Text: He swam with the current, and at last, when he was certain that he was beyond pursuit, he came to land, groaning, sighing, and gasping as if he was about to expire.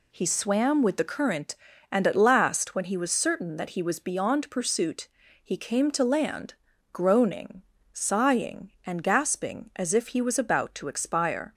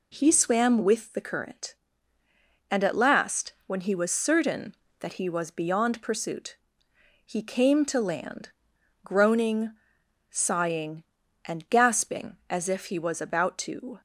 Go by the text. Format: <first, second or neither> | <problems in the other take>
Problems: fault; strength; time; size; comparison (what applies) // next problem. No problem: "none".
first | stops before "expire"; at 13.9 s